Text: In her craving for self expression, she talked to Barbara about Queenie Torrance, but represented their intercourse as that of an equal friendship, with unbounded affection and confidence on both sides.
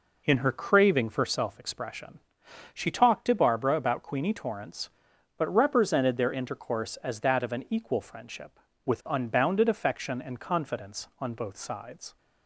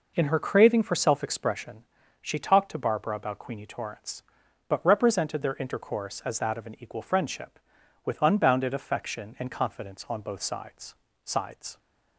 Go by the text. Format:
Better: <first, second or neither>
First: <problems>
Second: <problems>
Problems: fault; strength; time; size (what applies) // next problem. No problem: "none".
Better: first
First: none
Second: says "sides" twice; at 11.2 s